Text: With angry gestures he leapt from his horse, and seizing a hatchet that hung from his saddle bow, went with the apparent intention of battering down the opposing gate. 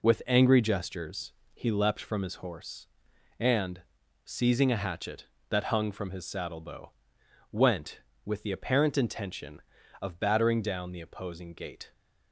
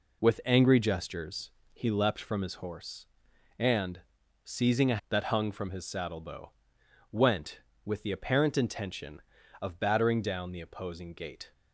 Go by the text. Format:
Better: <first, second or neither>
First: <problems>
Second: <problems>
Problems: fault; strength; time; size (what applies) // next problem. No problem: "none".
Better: first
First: pauses between "gestures" and "he"; slight; at 1.3 s; 0.20 s long // pauses between "and" and "seizing"; at 3.8 s; 0.42 s long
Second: pauses between "gestures" and "he"; slight; at 1.4 s; 0.22 s long // pauses between "and" and "seizing"; at 4.0 s; 0.42 s long // skips "hatchet"; at 5.0 s